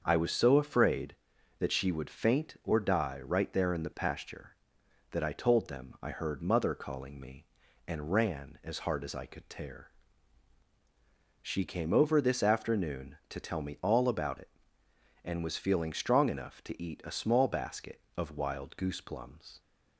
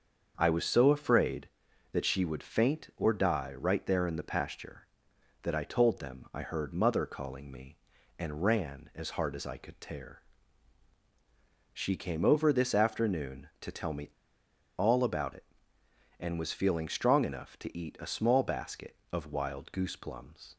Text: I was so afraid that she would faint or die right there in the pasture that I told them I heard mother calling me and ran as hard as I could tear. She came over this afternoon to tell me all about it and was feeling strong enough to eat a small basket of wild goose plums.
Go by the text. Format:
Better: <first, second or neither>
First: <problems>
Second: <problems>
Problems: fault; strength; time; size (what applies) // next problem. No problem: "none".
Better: first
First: starts louder than the rest; until 1.0 s; 6.5 dB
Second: starts louder than the rest; until 1.3 s; 6.5 dB // pauses between "me" and "all"; noticeable; at 14.0 s; 0.68 s long